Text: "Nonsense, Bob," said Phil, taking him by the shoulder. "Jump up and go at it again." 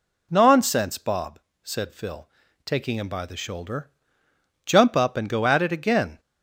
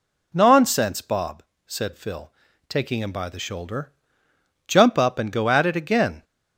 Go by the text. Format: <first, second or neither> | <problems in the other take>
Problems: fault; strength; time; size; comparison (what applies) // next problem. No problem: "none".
neither | none